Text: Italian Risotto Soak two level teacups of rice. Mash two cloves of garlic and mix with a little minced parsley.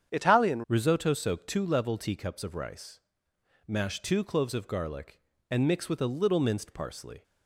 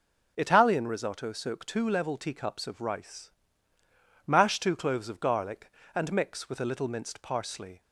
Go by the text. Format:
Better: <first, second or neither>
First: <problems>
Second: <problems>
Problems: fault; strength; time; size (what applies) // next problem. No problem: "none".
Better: second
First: starts louder than the rest; strong; until 1.1 s; 8.5 dB // changes voice at "Risotto"; from 0.6 s on; 6.6 s long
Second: none